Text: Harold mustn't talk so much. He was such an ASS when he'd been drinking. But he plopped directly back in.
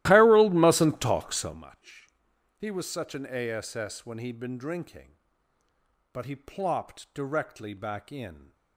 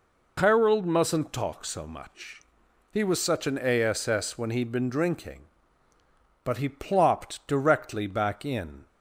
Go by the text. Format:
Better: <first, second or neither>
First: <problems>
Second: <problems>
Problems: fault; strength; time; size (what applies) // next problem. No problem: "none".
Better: second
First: starts louder than the rest; strong; until 1.6 s; 15.5 dB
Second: none